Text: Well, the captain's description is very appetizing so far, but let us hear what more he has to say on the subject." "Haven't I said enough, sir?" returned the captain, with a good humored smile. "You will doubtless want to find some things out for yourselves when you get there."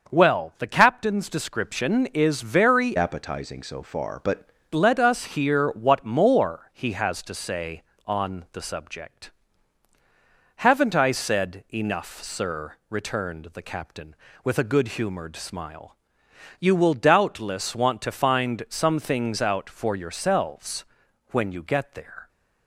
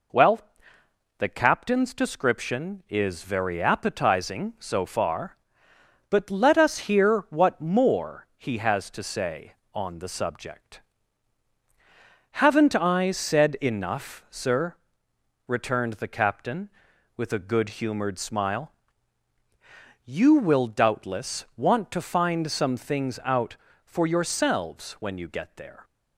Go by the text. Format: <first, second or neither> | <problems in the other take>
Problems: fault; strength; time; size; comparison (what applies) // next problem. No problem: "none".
second | starts louder than the rest; until 1.1 s; 6.5 dB // changes voice from "appetizing" to "but"; from 2.9 to 4.4 s; 1.5 s long // pauses between "yourselves" and "when"; noticeable; at 20.8 s; 0.46 s long